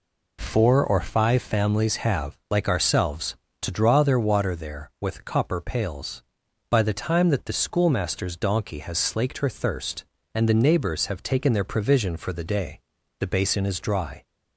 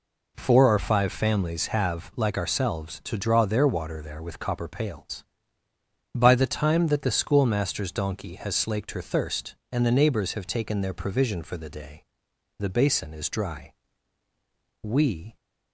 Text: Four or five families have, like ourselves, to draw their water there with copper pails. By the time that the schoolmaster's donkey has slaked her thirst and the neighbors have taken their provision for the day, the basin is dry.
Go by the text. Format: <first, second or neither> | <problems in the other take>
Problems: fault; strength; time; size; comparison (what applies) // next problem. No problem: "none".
first | goes on to say "We"; from 14.8 s on; 0.54 s long